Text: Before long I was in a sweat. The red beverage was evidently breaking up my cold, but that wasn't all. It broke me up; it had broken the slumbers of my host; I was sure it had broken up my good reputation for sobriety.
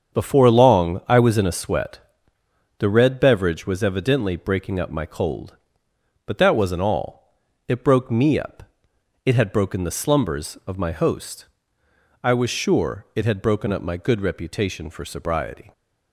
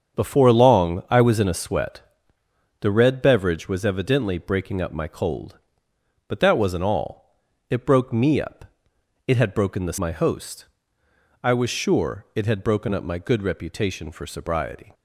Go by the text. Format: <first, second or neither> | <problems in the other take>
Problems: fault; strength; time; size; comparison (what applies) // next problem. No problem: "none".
first | starts louder than the rest; strong; until 1.2 s; 7.5 dB; strong in the first // skips "slumbers of"; at 9.9 s